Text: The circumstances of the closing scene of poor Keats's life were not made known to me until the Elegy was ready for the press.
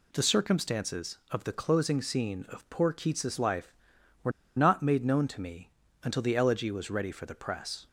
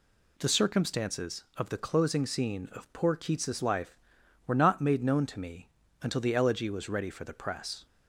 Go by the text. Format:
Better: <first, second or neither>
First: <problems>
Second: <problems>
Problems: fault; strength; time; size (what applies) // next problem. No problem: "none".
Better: second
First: pauses between "were" and "not"; slight; at 4.3 s; 0.27 s long // pauses between "me" and "until"; slight; at 5.7 s; 0.32 s long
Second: pauses between "me" and "until"; slight; at 5.6 s; 0.32 s long